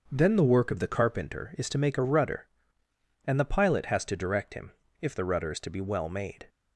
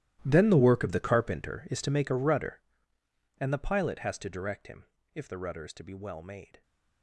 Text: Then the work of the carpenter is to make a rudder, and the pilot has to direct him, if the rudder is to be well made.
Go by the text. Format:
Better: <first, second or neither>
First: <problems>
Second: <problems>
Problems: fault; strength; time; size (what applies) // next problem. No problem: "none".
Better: first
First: starts louder than the rest; until 1.1 s; 6.5 dB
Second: gets quieter; strong; throughout; 17.5 dB // starts louder than the rest; strong; until 1.2 s; 14.5 dB